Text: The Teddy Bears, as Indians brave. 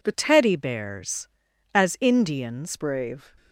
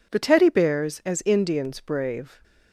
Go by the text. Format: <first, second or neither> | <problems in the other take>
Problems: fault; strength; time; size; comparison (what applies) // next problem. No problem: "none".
second | changes voice from "Teddy" to "Indians"; from 0.1 to 2.7 s; 2.6 s long